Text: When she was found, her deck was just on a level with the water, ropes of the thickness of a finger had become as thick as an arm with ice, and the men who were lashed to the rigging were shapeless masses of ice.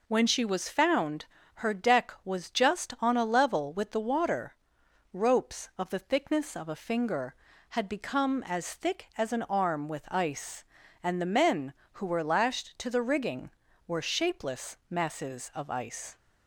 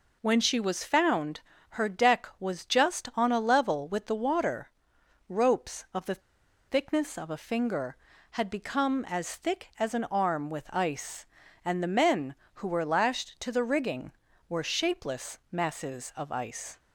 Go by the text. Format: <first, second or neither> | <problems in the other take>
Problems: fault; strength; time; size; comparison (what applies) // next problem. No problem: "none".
first | pauses between "the" and "thickness"; noticeable; at 6.2 s; 0.46 s long